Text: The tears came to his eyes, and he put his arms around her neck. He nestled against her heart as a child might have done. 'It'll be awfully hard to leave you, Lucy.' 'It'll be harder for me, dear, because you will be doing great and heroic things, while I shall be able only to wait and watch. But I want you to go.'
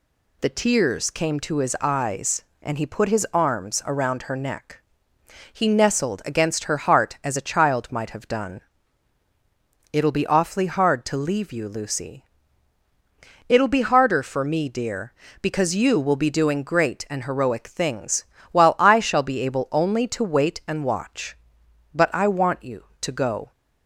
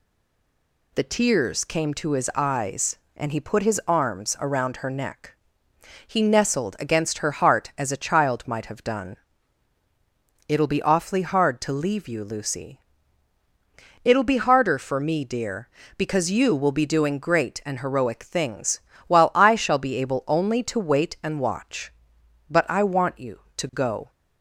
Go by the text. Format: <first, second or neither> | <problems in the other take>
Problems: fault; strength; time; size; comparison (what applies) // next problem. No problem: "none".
first | stays silent before the first word; slight; until 0.9 s; 0.9 s long